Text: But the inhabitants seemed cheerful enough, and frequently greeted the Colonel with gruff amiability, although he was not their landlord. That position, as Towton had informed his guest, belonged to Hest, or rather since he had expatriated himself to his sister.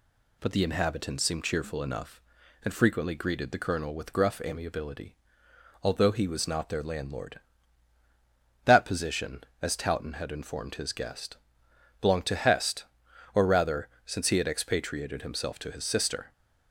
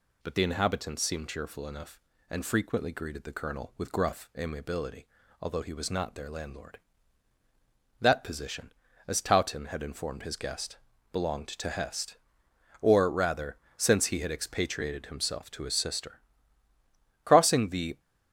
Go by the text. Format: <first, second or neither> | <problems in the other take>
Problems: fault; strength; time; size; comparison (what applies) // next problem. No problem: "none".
first | pauses between "rather" and "since"; slight; at 13.5 s; 0.20 s long; slight in the first // goes on to say "Crossing the"; noticeable; from 17.2 s on; 0.74 s long